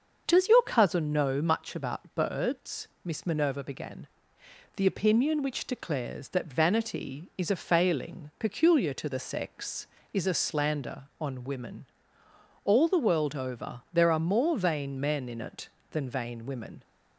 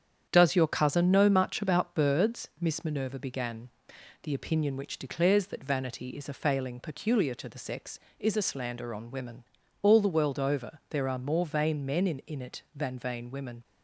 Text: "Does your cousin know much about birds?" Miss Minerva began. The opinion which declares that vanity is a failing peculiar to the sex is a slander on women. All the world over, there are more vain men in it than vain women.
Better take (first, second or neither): first